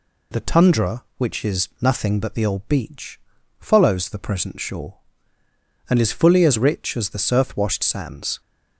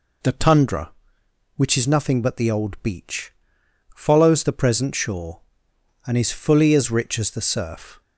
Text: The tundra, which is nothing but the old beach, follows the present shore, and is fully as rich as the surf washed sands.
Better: first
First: none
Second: stops before "washed sands"; at 8.0 s

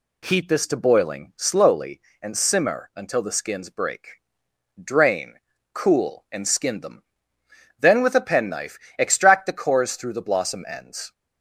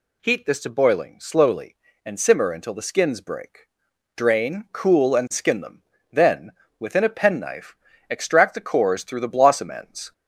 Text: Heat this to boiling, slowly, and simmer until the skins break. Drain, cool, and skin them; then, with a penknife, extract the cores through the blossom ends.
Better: first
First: none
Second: says "within" for "with"; at 6.7 s

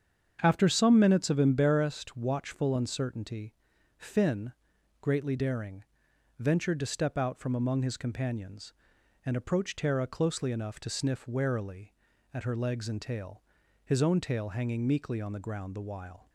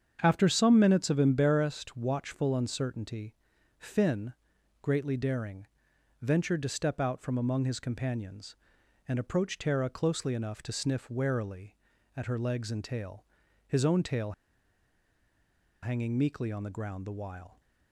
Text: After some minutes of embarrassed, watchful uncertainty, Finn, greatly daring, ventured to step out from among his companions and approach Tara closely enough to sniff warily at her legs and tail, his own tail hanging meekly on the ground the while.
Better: first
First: starts louder than the rest; strong; until 1.4 s; 7.5 dB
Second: starts louder than the rest; strong; until 1.2 s; 7.5 dB // pauses between "tail" and "hanging"; strong; at 14.3 s; 1.5 s long

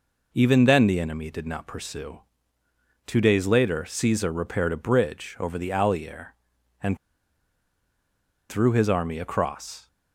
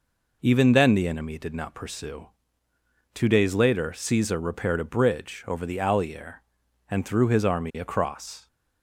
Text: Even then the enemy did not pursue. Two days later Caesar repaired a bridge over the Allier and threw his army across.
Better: second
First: pauses between "and" and "threw"; strong; at 6.9 s; 1.5 s long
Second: none

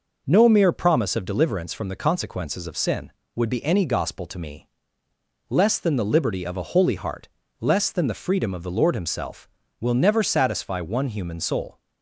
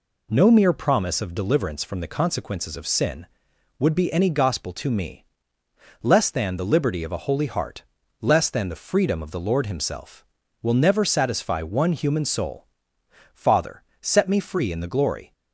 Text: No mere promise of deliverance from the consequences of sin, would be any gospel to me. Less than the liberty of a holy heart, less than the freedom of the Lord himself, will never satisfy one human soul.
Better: first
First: none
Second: goes on to say "Father set me free in the glory"; strong; from 13.3 s on; 1.9 s long

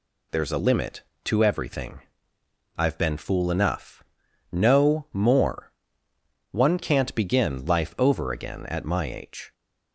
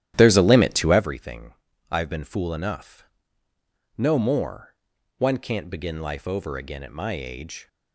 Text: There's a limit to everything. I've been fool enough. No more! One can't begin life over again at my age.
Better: first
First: none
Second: starts louder than the rest; strong; until 1.1 s; 12.5 dB

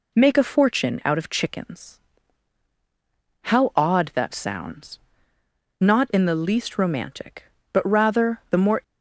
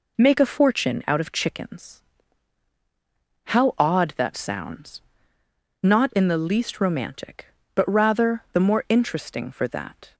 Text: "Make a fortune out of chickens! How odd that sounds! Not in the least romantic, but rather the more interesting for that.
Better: second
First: stops before "interesting for that"; at 8.8 s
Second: none

